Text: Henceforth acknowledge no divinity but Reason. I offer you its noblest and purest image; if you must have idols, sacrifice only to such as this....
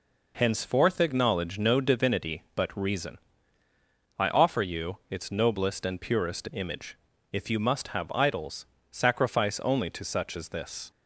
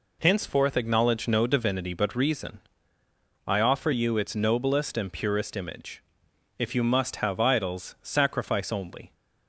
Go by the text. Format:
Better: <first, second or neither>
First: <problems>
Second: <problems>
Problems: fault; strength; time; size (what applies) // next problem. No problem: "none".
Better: first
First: none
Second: stops before "to such as this"; at 9.1 s